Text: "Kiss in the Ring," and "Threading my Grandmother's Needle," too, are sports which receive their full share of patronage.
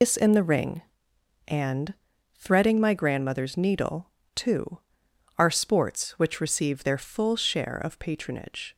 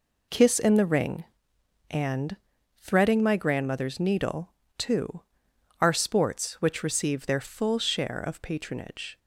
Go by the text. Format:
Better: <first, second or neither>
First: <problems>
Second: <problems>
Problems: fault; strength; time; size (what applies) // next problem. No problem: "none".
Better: second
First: loses the start of "Kiss"; at 0.0 s; 135 ms // pauses between "and" and "Threading"; at 1.9 s; 0.40 s long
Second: pauses between "and" and "Threading"; at 2.3 s; 0.40 s long